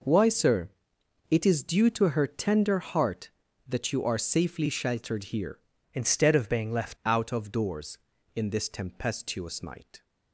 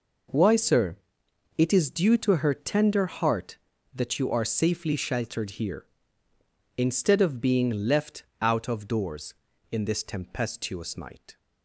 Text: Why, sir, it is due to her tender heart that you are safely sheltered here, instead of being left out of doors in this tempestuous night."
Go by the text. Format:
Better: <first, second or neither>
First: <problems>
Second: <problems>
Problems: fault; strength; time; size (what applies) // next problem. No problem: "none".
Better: second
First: changes voice from "instead" to "left"; from 5.9 to 6.9 s; 1.0 s long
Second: none